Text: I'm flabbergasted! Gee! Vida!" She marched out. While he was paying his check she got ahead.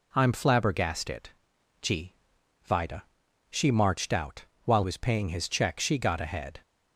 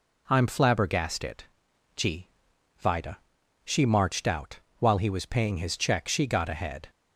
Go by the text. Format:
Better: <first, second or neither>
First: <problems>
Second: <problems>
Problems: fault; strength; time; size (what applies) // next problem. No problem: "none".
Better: second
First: skips "he"; at 4.8 s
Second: none